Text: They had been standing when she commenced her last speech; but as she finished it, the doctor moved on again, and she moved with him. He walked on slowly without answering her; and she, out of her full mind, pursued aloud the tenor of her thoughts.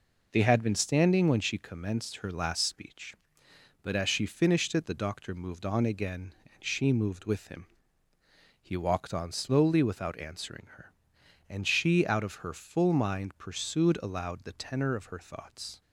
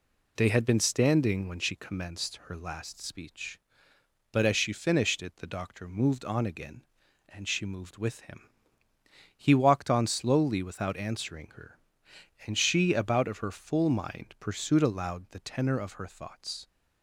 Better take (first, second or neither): first